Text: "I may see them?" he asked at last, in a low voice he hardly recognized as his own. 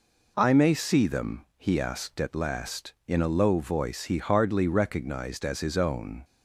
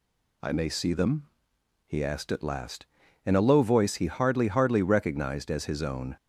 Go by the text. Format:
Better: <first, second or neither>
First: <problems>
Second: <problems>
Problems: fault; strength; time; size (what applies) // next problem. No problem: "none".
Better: first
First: none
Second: says "hardly" twice; at 4.4 s